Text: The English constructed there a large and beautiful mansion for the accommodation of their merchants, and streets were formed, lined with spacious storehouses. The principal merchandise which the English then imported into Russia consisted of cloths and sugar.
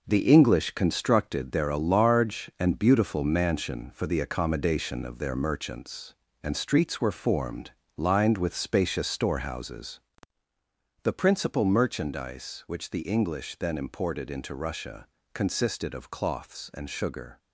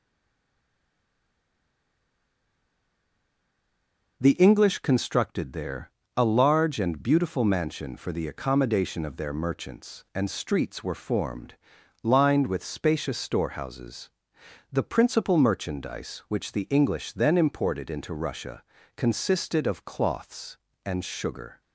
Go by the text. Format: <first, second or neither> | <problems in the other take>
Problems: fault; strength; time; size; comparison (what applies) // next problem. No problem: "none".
first | stays silent before the first word; strong; until 4.2 s; 4.2 s long // pauses between "there" and "a"; slight; at 5.9 s; 0.26 s long // pauses between "Russia" and "consisted"; slight; at 18.6 s; 0.32 s long; slight in the first